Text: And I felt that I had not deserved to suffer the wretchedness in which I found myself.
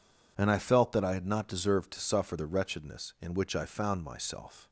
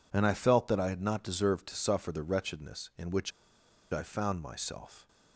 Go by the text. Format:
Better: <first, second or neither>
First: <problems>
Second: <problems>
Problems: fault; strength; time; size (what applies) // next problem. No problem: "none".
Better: first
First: none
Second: pauses between "which" and "I"; noticeable; at 3.3 s; 0.61 s long